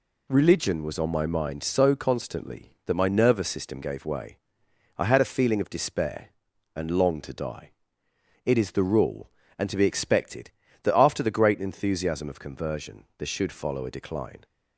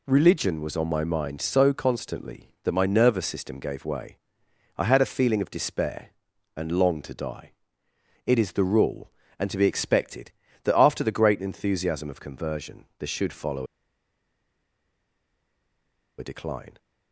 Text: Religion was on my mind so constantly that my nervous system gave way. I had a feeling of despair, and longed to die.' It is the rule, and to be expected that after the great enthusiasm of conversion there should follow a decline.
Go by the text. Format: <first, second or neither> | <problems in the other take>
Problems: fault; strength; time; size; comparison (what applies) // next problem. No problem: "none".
first | pauses between "follow" and "a"; strong; at 13.6 s; 2.5 s long